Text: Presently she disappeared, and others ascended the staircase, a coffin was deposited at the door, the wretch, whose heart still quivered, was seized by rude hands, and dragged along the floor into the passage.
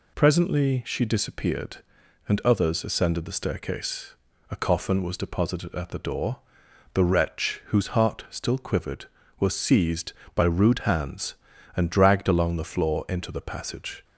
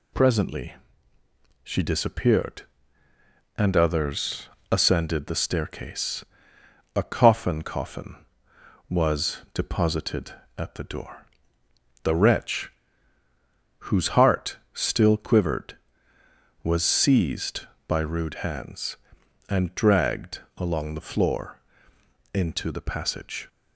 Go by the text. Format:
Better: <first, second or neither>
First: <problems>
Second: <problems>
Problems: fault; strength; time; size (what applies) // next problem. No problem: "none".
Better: first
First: none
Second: pauses between "Presently" and "she"; noticeable; at 0.7 s; 0.90 s long // pauses between "others" and "ascended"; slight; at 4.4 s; 0.22 s long // says "coffin" twice; at 7.6 s // pauses between "was" and "deposited"; slight; at 9.3 s; 0.16 s long // pauses between "dragged" and "along"; slight; at 20.4 s; 0.16 s long // pauses between "floor" and "into"; noticeable; at 21.5 s; 0.74 s long